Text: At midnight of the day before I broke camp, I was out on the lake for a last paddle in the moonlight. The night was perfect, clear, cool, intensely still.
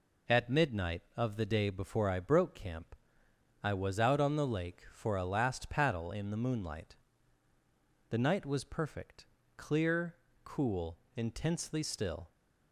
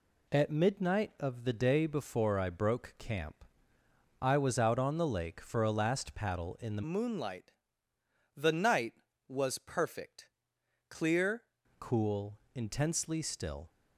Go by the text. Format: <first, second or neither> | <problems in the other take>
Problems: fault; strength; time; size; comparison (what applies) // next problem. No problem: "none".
first | changes voice from "moonlight" to "clear"; from 6.8 to 11.4 s; 4.6 s long